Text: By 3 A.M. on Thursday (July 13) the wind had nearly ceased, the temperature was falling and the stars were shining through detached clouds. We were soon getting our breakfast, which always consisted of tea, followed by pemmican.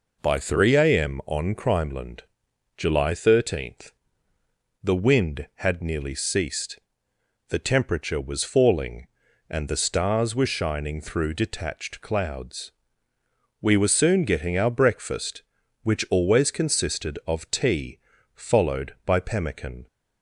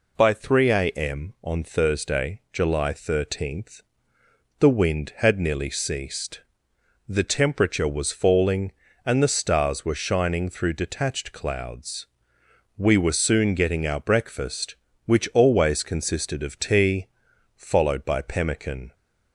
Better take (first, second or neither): second